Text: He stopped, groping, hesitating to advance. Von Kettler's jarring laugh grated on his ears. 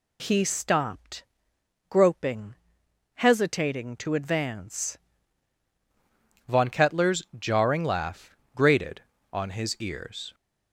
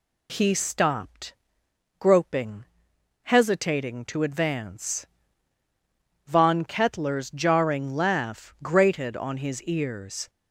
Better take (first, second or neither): second